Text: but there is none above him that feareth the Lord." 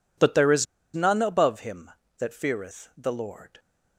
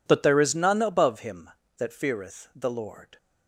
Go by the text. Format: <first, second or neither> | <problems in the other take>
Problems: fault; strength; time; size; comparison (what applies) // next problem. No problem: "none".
second | pauses between "is" and "none"; slight; at 0.6 s; 0.29 s long